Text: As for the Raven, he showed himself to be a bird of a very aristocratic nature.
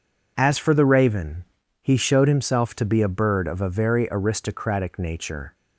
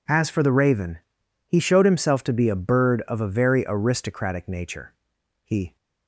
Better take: first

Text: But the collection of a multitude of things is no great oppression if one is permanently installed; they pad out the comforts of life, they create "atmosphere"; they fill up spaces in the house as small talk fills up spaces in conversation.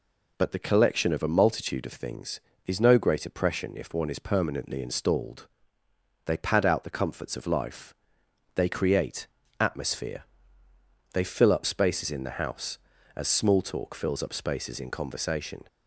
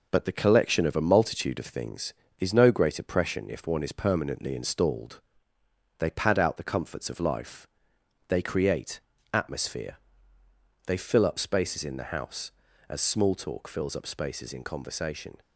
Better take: first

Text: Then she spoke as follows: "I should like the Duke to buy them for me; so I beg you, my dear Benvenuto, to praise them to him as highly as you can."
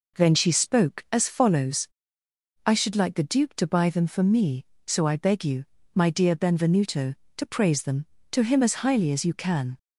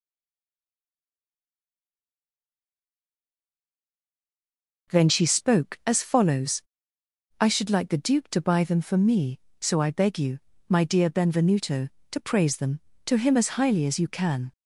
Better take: first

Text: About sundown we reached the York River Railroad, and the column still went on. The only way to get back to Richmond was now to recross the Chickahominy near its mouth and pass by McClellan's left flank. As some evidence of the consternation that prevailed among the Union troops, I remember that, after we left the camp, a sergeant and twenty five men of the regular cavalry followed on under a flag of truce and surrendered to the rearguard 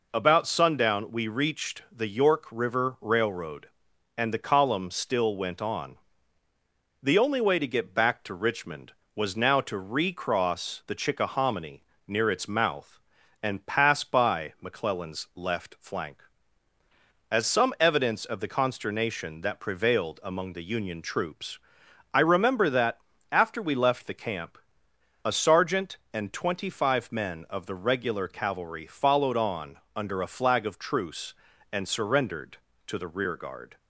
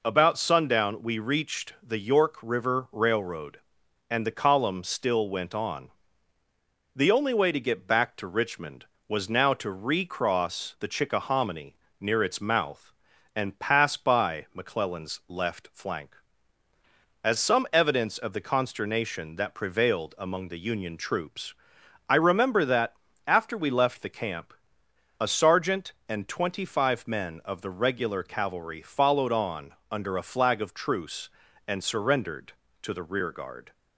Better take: neither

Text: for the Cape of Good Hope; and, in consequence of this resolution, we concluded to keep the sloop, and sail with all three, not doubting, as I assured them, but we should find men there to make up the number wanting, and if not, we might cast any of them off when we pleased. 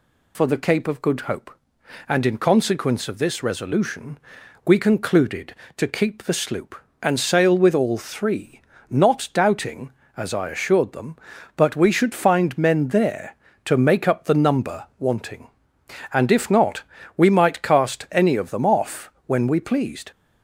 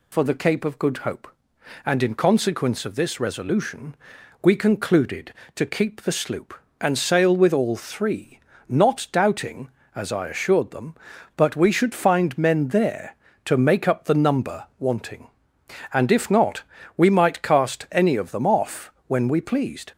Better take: neither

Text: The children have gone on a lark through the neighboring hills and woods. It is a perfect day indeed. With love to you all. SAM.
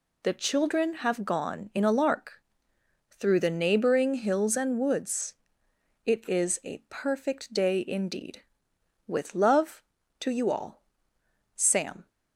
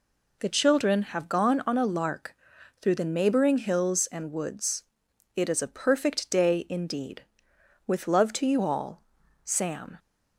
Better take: second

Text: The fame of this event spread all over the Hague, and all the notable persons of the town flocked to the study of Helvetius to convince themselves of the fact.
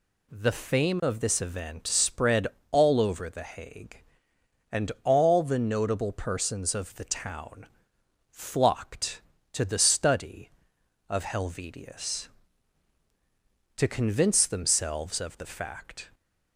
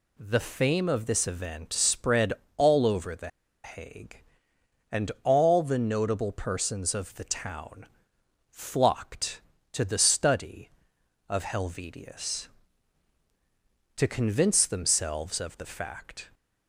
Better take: first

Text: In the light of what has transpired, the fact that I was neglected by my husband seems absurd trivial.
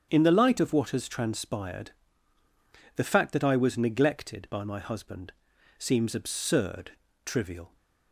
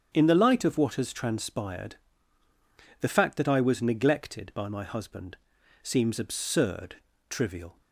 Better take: neither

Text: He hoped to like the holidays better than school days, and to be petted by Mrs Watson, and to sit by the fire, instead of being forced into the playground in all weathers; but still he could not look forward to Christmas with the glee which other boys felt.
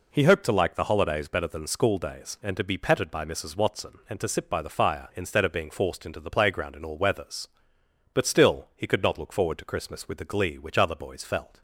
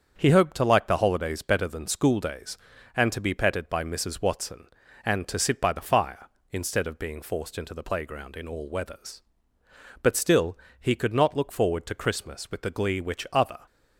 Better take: first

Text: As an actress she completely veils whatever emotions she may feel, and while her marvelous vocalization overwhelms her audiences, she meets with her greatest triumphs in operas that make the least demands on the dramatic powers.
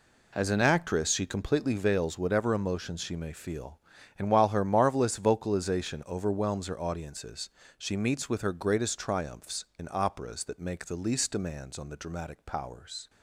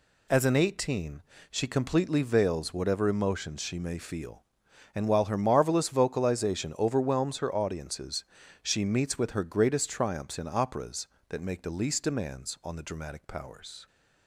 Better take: first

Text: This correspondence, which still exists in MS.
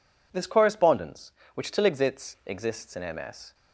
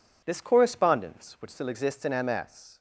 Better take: second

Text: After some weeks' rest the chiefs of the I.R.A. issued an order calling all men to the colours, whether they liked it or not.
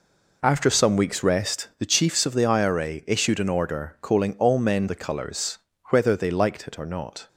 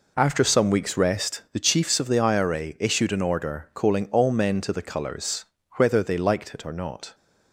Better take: second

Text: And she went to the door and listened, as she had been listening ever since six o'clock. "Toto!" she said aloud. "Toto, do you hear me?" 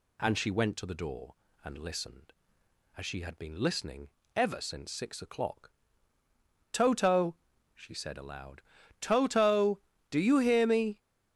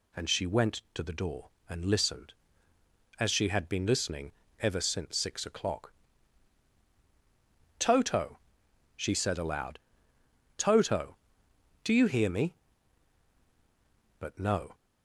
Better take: first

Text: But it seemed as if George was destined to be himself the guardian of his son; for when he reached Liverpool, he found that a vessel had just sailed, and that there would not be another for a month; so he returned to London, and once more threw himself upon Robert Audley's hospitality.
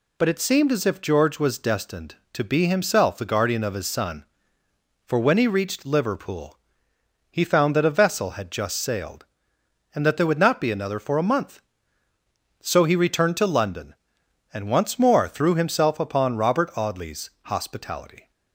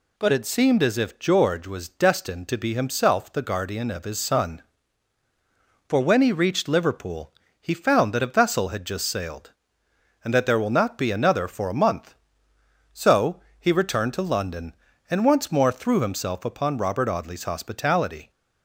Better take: first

